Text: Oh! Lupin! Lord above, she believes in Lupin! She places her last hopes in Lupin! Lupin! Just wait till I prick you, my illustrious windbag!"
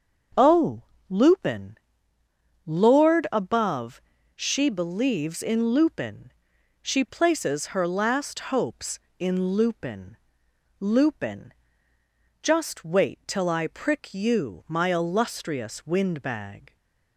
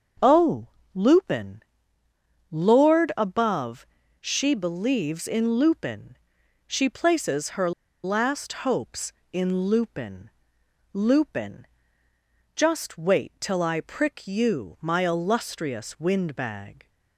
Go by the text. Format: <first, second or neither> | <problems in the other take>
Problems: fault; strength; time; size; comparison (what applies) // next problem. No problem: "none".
first | starts louder than the rest; until 1.4 s; 6.5 dB; also in the first // pauses between "her" and "last"; slight; at 7.7 s; 0.33 s long